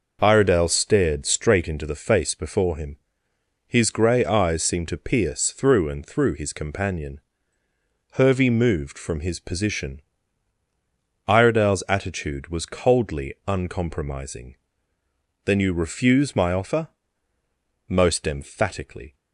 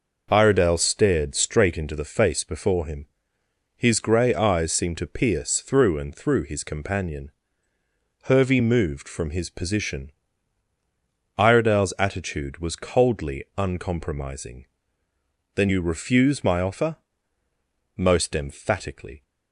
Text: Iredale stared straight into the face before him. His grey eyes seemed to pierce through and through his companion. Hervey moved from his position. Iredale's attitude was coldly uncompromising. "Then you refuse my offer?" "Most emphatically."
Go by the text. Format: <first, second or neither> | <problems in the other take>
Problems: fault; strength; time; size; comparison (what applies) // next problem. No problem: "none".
neither | none